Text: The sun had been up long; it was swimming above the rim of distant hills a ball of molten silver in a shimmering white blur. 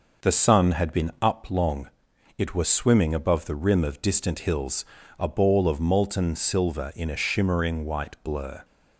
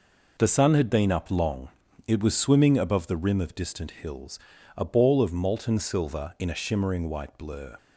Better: neither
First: pauses between "hills" and "a"; slight; at 4.8 s; 0.32 s long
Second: pauses between "hills" and "a"; at 4.3 s; 0.40 s long

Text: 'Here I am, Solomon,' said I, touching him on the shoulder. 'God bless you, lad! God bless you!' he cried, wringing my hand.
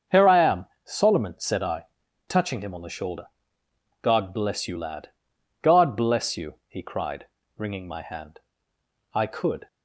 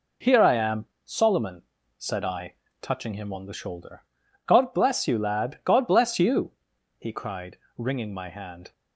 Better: second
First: starts louder than the rest; until 1.2 s; 6.5 dB // goes on to say "I could"; from 9.1 s on; 0.52 s long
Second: none

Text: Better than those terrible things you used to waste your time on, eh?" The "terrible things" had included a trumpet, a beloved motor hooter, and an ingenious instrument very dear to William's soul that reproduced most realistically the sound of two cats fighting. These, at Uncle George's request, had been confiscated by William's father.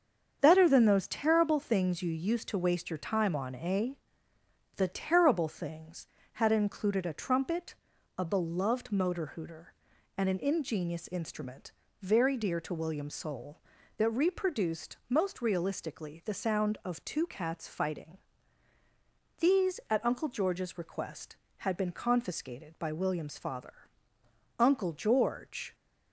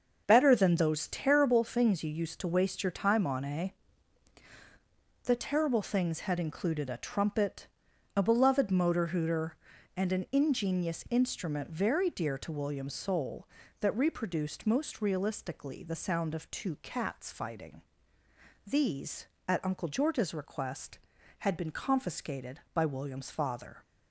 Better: second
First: starts louder than the rest; strong; until 1.4 s; 7 dB // pauses between "instrument" and "very"; slight; at 11.7 s; 0.28 s long // goes on to say "Uncle George"; noticeable; from 24.5 s on; 1.1 s long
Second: starts louder than the rest; until 1.2 s; 6.5 dB

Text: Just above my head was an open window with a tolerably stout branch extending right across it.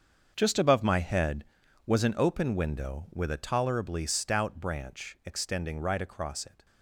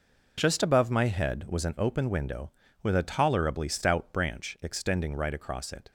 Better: second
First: gets quieter; strong; throughout; 13 dB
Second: none

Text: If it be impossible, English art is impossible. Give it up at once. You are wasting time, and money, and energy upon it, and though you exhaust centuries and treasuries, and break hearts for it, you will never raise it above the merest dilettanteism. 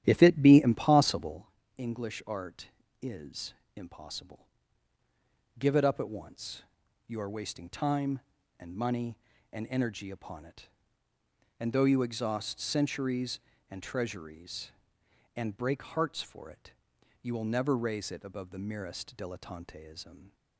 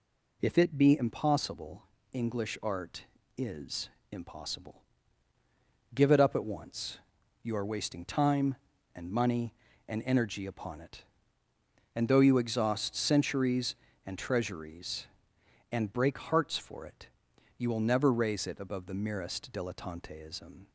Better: second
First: starts louder than the rest; strong; until 1.4 s; 11.5 dB // pauses between "is" and "impossible"; slight; at 3.5 s; 0.20 s long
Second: pauses between "is" and "impossible"; slight; at 3.8 s; 0.20 s long

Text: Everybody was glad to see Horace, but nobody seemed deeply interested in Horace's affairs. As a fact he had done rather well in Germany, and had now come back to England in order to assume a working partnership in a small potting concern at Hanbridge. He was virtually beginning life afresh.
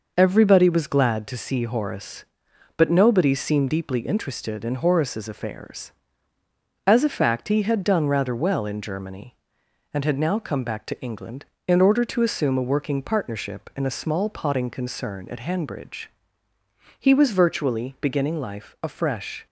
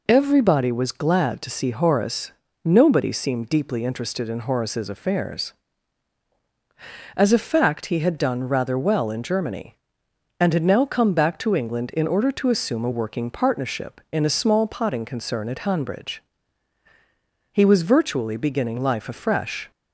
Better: first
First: none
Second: skips "but"; at 2.4 s

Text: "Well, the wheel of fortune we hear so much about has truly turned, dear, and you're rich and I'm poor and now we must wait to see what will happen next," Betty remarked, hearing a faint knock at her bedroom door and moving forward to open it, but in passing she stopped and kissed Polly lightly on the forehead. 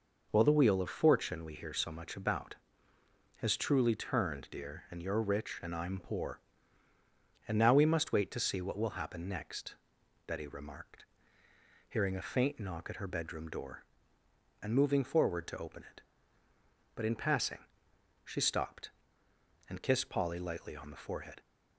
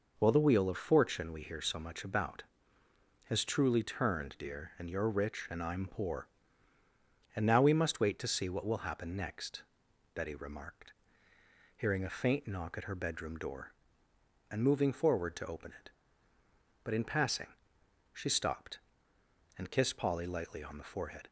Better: neither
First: pauses between "passing" and "she"; noticeable; at 17.5 s; 0.66 s long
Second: pauses between "passing" and "she"; noticeable; at 17.4 s; 0.66 s long

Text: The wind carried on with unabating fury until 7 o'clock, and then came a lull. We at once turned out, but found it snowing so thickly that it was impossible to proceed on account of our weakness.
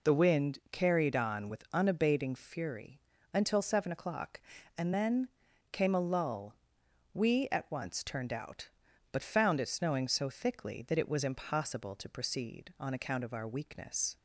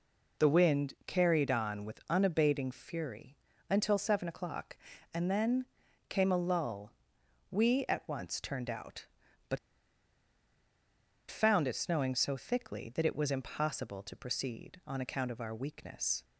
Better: first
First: pauses between "fury" and "until"; slight; at 2.9 s; 0.34 s long // pauses between "then" and "came"; at 5.2 s; 0.44 s long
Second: pauses between "fury" and "until"; slight; at 3.3 s; 0.34 s long // pauses between "then" and "came"; at 5.6 s; 0.44 s long // pauses between "but" and "found"; strong; at 9.5 s; 1.7 s long

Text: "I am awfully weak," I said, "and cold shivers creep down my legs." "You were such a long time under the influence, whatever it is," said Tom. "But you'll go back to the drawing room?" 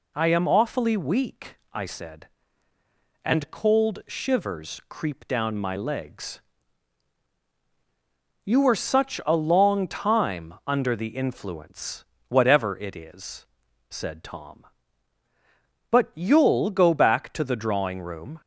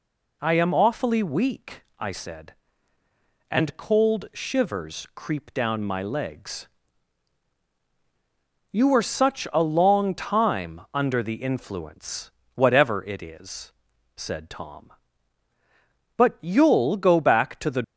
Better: first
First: none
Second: stops before "drawing room"; at 17.8 s

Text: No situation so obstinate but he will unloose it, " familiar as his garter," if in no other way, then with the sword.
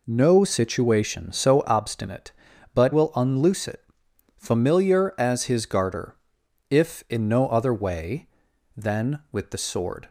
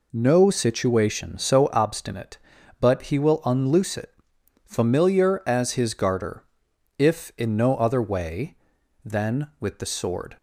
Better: second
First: skips "he"; at 2.9 s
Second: none

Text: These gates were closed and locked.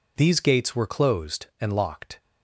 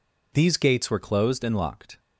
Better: first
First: none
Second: changes voice at "were"; from 0.8 s on; 1.1 s long

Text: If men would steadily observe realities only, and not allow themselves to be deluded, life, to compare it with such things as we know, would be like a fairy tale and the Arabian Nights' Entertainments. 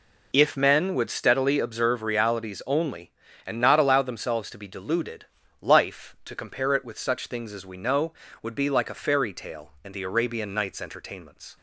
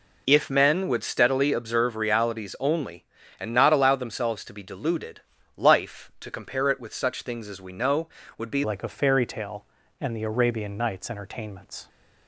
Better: first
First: none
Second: changes voice at "like"; from 8.6 s on; 3.2 s long

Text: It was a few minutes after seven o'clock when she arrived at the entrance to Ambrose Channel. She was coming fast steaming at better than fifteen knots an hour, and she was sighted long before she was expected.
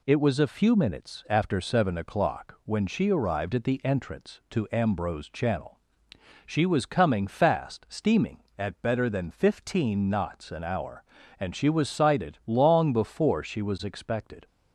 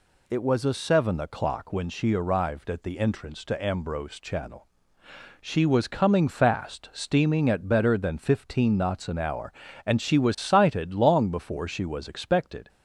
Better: first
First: none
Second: skips "few minutes after"; at 0.7 s

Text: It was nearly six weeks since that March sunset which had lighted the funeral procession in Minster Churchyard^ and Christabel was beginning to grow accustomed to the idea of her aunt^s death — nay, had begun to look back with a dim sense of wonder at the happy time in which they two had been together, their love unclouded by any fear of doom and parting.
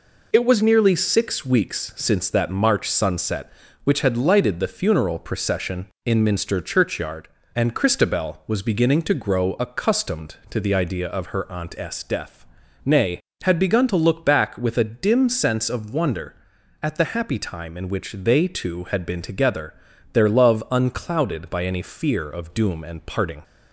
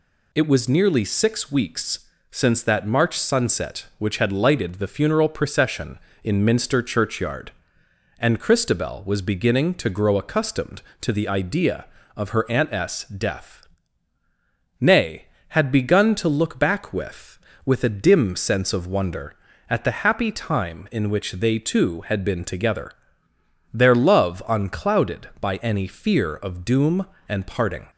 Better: first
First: none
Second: pauses between "weeks" and "since"; slight; at 2.0 s; 0.24 s long // says "with" twice; at 17.6 s

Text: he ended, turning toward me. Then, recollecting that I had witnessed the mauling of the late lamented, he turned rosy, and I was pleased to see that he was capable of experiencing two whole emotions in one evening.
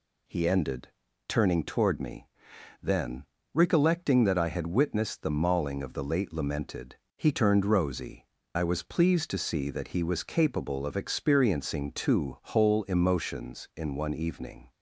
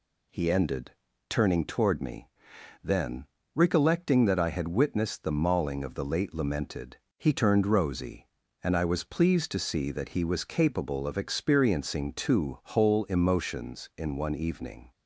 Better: second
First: skips "and"; at 8.4 s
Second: none

